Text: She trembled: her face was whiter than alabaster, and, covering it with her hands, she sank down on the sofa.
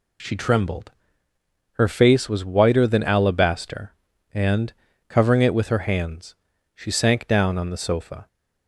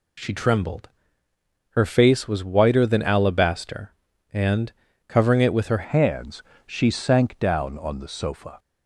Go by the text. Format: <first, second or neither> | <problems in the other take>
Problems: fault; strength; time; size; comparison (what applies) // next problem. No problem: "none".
first | changes voice at "hands"; from 5.8 s on; 2.7 s long